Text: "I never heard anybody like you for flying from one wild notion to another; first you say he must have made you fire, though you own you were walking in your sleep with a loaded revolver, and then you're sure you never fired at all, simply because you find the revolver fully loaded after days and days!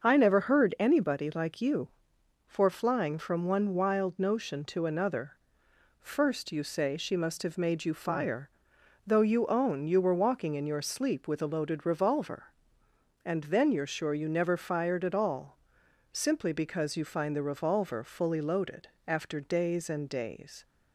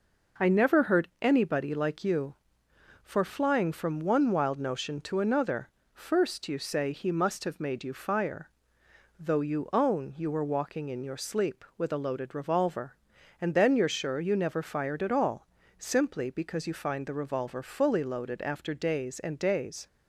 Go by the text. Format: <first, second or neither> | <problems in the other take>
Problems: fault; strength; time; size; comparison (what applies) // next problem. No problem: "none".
second | starts louder than the rest; until 1.1 s; 6.5 dB // says "she" for "he"; at 6.9 s // pauses between "loaded" and "after"; slight; at 18.8 s; 0.18 s long